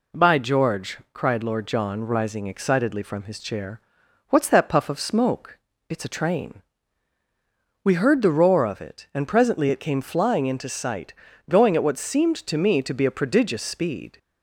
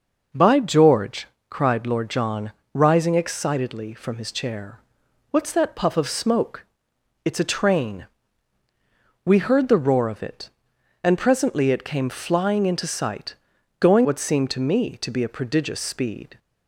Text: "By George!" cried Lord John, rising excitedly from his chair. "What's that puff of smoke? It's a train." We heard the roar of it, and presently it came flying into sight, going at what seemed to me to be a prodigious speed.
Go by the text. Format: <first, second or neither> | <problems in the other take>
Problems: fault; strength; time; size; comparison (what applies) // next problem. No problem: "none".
first | skips "at"; at 14.0 s